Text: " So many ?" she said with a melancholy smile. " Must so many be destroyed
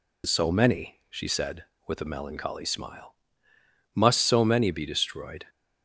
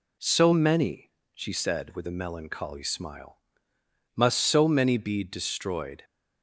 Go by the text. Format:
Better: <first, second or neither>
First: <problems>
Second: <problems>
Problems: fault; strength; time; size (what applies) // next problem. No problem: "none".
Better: neither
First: none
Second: none